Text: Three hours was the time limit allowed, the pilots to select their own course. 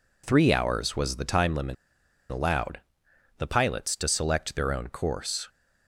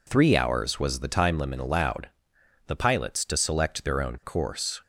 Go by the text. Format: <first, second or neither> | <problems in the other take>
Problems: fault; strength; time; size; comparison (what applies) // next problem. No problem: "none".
second | pauses between "limit" and "allowed"; noticeable; at 1.7 s; 0.56 s long